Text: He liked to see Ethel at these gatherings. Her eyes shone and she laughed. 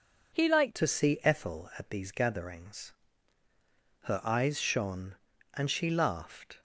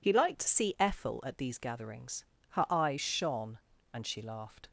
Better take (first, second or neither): second